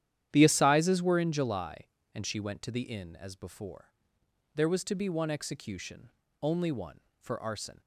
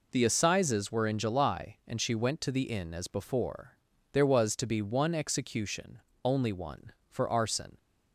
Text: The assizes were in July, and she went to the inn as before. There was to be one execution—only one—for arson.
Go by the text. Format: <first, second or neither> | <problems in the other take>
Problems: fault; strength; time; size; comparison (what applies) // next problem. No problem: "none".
second | starts louder than the rest; strong; until 1.4 s; 10.5 dB